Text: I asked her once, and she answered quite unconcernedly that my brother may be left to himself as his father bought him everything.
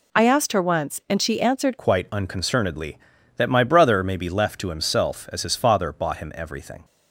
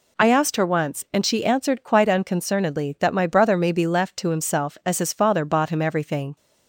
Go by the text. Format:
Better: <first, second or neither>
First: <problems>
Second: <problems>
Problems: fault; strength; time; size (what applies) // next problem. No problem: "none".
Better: second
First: changes voice at "quite"; from 1.7 s on; 5.1 s long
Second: none